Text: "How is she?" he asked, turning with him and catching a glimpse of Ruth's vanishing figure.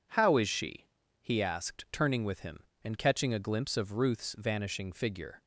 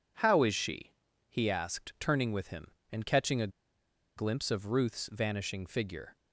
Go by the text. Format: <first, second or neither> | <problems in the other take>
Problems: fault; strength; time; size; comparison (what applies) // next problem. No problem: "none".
first | pauses between "a" and "glimpse"; noticeable; at 3.4 s; 0.67 s long